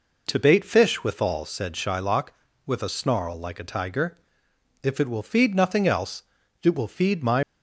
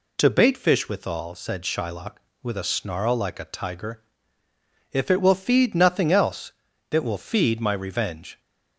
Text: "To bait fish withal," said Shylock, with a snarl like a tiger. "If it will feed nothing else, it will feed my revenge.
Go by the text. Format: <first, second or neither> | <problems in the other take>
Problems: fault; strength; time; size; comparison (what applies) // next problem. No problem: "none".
second | stops before "revenge"; at 7.4 s